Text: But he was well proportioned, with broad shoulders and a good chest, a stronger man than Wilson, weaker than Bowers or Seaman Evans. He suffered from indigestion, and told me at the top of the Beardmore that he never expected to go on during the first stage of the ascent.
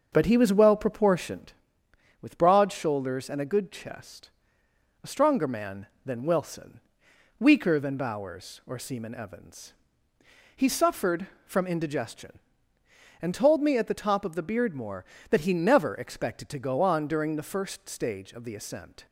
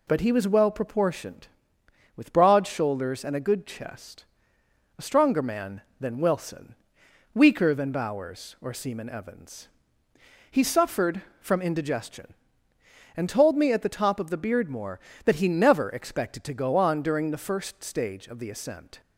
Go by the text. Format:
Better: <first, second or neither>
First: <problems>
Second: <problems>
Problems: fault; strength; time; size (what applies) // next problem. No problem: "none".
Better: second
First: starts louder than the rest; until 1.5 s; 6.5 dB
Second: none